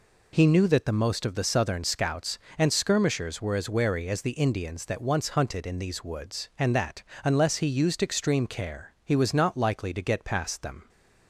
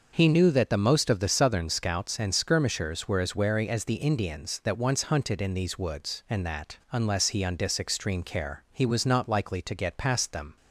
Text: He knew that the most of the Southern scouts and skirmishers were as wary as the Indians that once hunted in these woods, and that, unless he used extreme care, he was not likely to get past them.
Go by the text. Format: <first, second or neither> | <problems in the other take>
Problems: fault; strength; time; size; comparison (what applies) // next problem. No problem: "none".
first | starts louder than the rest; noticeable; until 1.1 s; 6 dB // says "undis" for "used"; at 7.4 s